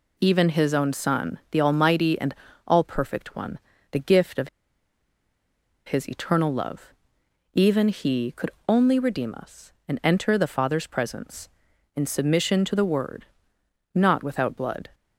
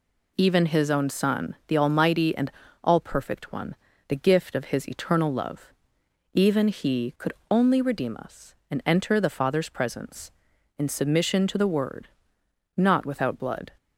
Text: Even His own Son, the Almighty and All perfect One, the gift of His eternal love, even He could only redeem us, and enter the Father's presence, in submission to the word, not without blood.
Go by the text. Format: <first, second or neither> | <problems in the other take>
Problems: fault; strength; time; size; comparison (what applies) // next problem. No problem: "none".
second | pauses between "and" and "All"; slight; at 2.3 s; 0.34 s long; slight in the second // pauses between "of" and "His"; strong; at 4.4 s; 1.3 s long // pauses between "could" and "only"; slight; at 8.4 s; 0.18 s long; slight in the second